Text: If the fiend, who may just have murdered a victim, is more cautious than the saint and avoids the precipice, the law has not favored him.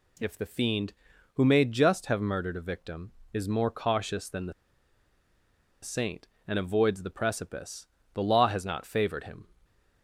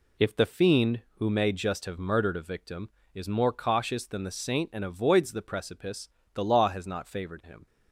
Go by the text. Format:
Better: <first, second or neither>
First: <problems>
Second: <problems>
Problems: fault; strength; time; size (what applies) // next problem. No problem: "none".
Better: second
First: pauses between "the" and "saint"; strong; at 4.5 s; 1.3 s long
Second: none